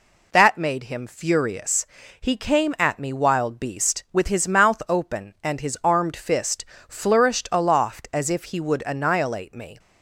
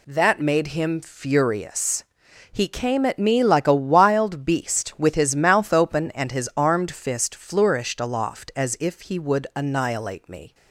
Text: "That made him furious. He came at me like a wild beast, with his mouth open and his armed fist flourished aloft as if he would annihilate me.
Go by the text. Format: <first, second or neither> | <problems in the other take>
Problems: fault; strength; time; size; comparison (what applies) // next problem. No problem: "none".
second | skips "like a"; at 3.1 s // pauses between "fist" and "flourished"; slight; at 6.6 s; 0.24 s long